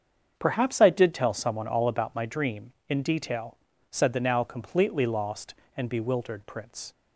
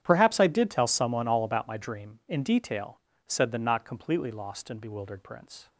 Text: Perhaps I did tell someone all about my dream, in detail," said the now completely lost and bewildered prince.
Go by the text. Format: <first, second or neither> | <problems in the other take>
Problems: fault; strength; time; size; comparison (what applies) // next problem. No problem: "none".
first | starts louder than the rest; strong; until 1.0 s; 9 dB; strong in the first // says "not" for "now"; at 3.5 s